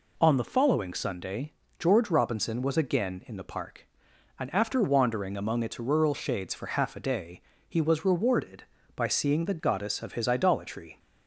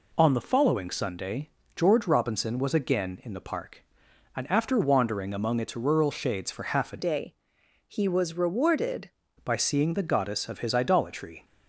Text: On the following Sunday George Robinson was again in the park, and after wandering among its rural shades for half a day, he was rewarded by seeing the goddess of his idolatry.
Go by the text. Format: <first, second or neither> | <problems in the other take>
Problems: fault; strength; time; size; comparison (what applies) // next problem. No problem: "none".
first | pauses between "Sunday" and "George"; slight; at 1.4 s; 0.26 s long; slight in the first // changes voice from "day" to "rewarded"; from 6.9 to 9.1 s; 2.2 s long